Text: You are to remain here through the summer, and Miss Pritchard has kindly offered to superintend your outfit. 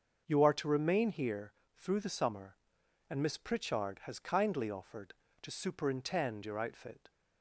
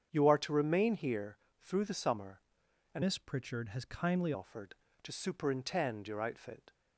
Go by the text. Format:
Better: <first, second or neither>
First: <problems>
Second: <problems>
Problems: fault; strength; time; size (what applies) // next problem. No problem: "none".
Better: first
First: starts louder than the rest; until 1.2 s; 6.5 dB // pauses between "here" and "through"; slight; at 1.5 s; 0.24 s long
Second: starts louder than the rest; strong; until 1.1 s; 8 dB // pauses between "here" and "through"; slight; at 1.3 s; 0.24 s long // changes voice from "Miss" to "kindly"; from 3.0 to 4.3 s; 1.3 s long